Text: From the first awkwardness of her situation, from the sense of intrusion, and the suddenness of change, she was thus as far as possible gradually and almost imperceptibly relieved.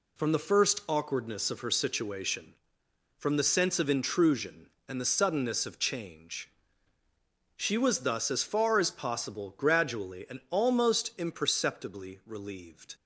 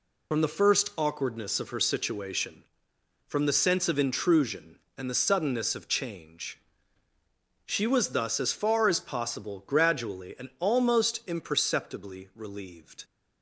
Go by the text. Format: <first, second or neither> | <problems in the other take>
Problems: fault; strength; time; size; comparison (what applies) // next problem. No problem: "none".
first | loses the start of "From"; at 0.3 s; 45 ms